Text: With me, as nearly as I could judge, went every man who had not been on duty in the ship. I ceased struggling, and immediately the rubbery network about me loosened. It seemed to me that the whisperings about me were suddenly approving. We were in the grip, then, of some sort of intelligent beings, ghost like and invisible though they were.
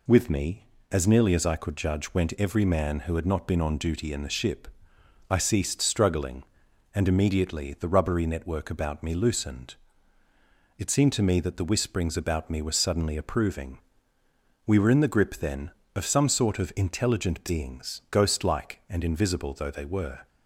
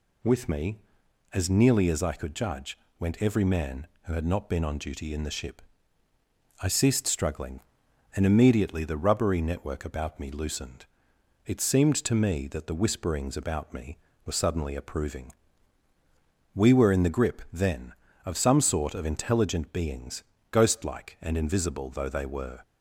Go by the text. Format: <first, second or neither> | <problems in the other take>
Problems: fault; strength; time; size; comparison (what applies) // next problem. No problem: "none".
neither | none